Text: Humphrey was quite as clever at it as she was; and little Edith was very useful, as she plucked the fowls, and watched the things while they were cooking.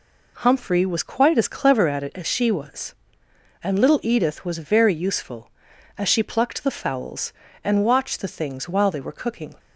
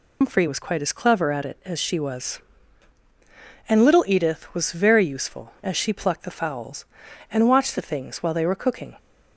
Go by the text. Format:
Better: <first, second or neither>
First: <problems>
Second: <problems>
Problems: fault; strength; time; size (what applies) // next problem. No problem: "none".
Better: first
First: none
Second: loses the start of "Humphrey"; at 0.2 s; 140 ms